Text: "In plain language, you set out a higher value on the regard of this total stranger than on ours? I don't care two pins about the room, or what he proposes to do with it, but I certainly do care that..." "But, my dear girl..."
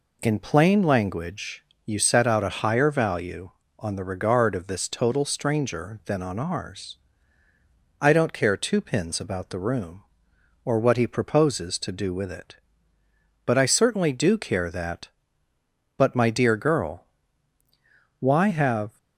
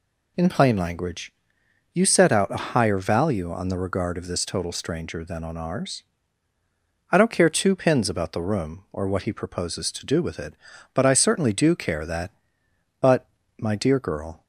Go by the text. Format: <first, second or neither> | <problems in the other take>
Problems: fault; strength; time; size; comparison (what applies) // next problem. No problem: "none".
second | goes on to say "Why have"; noticeable; from 18.1 s on; 0.78 s long